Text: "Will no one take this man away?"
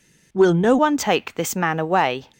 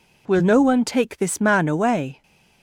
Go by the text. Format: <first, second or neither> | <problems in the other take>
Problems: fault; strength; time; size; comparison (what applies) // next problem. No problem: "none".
second | changes voice at "one"; from 0.7 s on; 1.5 s long